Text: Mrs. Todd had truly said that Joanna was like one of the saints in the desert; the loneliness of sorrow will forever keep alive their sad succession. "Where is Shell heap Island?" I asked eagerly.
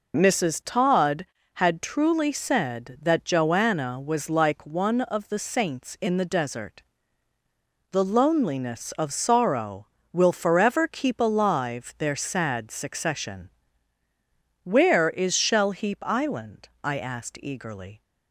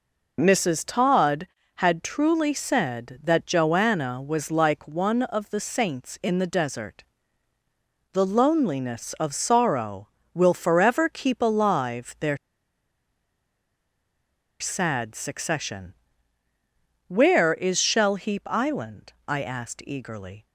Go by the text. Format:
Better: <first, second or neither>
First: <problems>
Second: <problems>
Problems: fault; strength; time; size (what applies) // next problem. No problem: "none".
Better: first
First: none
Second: pauses between "their" and "sad"; strong; at 12.3 s; 2.2 s long